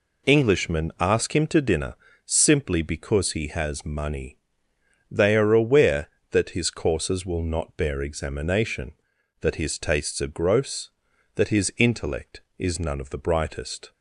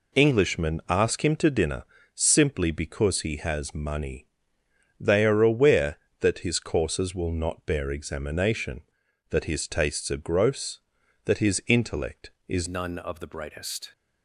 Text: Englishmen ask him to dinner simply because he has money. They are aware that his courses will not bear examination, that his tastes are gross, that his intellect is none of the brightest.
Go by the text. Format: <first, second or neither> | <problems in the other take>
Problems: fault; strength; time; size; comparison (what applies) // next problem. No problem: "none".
first | pauses between "dinner" and "simply"; slight; at 1.8 s; 0.30 s long; slight in the first // changes voice at "none"; from 12.6 s on; 1.3 s long